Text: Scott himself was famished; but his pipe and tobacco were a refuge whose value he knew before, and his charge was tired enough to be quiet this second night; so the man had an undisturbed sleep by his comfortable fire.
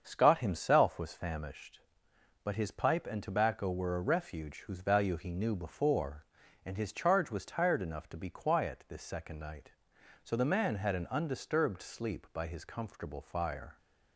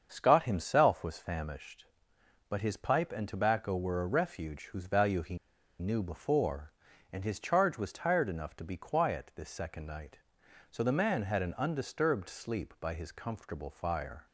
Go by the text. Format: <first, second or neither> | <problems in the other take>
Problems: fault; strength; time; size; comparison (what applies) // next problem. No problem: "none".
first | starts louder than the rest; until 1.1 s; 7 dB; also in the first // pauses between "he" and "knew"; at 5.3 s; 0.42 s long